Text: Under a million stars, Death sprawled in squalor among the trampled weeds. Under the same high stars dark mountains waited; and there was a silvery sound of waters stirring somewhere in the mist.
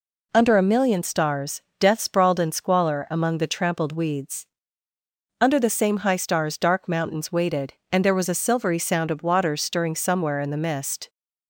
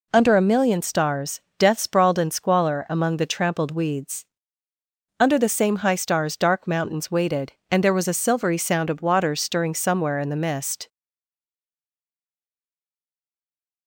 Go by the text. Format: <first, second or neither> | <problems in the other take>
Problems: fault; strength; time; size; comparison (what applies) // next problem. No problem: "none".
first | stays silent after the last word; strong; from 10.8 s on; 3.0 s long